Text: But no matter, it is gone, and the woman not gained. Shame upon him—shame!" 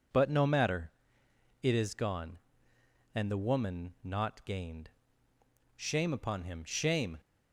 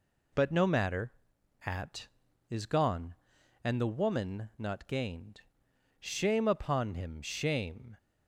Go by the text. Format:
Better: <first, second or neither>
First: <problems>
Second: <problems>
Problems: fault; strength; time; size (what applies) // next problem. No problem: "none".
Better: first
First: none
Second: says "at" for "it"; at 1.6 s